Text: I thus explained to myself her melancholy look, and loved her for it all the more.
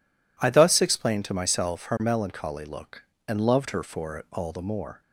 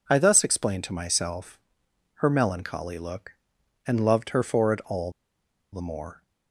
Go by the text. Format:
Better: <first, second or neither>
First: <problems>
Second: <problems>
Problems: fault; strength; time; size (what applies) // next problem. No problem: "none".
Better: first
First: none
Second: pauses between "myself" and "her"; noticeable; at 1.5 s; 0.62 s long // pauses between "all" and "the"; noticeable; at 5.0 s; 0.62 s long